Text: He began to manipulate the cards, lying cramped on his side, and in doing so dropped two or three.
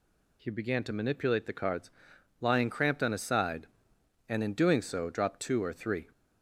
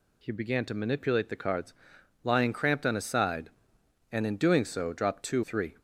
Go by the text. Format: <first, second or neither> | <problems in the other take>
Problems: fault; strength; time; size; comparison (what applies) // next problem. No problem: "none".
first | skips "or"; at 5.4 s